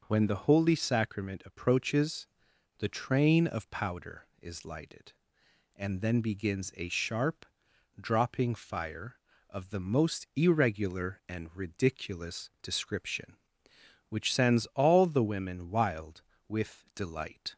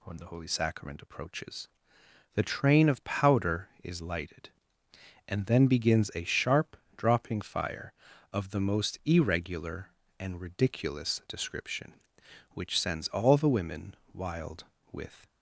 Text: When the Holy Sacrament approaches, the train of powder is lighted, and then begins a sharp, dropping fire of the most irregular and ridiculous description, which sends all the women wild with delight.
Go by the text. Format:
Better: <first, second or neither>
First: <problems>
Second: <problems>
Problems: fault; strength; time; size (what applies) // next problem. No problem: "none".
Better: first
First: none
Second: pauses between "women" and "wild"; slight; at 13.9 s; 0.18 s long // stops before "delight"; at 15.2 s